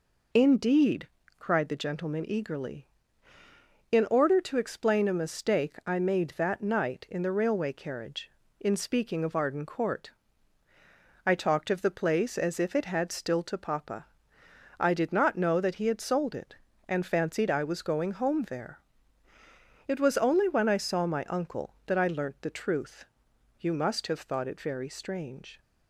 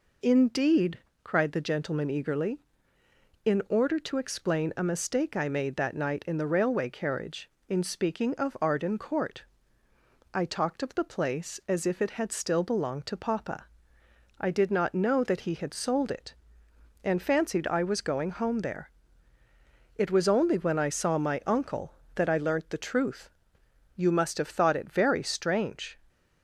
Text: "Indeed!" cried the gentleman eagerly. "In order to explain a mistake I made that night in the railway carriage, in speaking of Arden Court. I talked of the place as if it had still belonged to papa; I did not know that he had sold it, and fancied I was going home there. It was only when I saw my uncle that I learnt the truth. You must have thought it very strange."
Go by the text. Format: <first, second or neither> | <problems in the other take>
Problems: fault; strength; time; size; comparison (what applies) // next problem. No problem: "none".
second | skips "belonged"; at 13.4 s